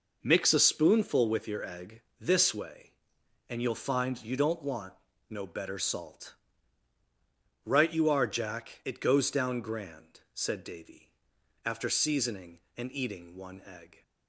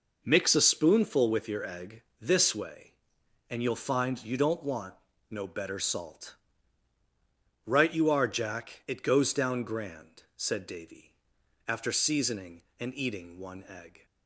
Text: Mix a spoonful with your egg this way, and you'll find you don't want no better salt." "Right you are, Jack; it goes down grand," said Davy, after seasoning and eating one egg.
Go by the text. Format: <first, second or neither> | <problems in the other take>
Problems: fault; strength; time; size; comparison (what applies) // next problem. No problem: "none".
neither | pauses between "egg" and "this"; slight; the same in both // pauses between "want" and "no"; the same in both